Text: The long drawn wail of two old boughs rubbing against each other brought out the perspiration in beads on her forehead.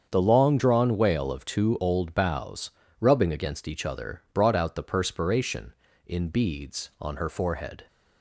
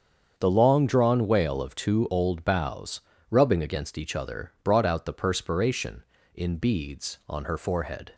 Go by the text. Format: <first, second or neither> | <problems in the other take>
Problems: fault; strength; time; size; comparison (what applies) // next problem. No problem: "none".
neither | starts louder than the rest; strong; the same in both // pauses between "boughs" and "rubbing"; slight; the same in both